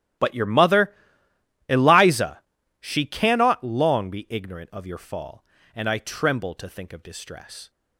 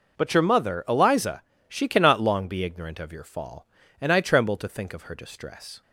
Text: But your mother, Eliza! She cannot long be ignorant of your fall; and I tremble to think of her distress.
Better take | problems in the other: second | starts louder than the rest; strong; until 1.9 s; 13 dB // skips "her"; at 7.0 s

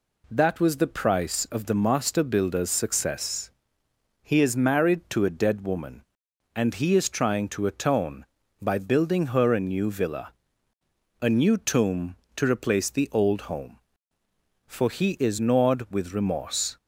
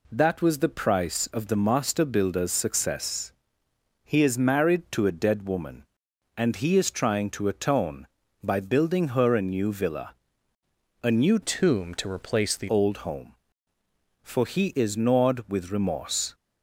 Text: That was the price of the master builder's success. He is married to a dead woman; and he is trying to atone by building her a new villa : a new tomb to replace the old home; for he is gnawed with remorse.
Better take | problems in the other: first | changes voice from "tomb" to "the"; from 11.4 to 12.6 s; 1.2 s long

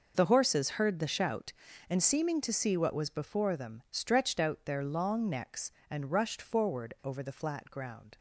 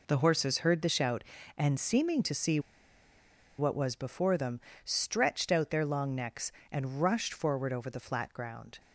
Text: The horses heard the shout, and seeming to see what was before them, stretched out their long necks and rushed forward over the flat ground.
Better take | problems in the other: first | pauses between "see" and "what"; at 2.5 s; 0.99 s long

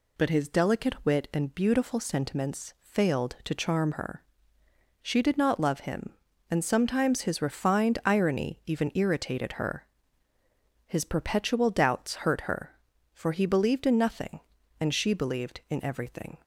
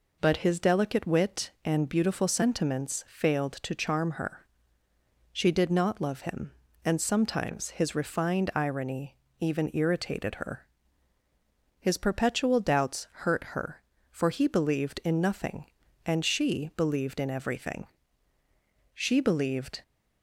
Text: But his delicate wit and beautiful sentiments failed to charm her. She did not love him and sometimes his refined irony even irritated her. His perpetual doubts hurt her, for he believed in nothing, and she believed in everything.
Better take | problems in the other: first | pauses between "irony" and "even"; slight; at 9.1 s; 0.24 s long // goes on to say "She believed"; noticeable; from 18.9 s on; 0.90 s long

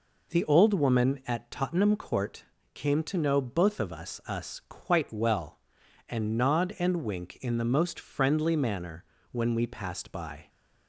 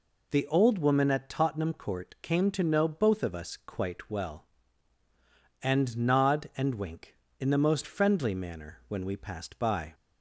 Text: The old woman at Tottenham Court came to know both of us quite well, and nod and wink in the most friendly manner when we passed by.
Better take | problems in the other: second | pauses between "Court" and "came"; slight; at 2.4 s; 0.30 s long // says "us" twice; at 4.2 s // pauses between "manner" and "when"; slight; at 9.0 s; 0.28 s long

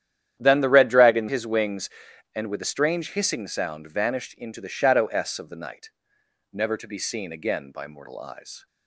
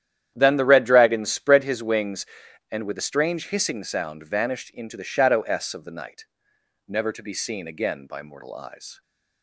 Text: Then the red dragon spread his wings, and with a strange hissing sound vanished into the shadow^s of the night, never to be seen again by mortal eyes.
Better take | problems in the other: second | starts louder than the rest; strong; until 1.3 s; 10.5 dB; strong in the second // skips "spread"; at 1.2 s

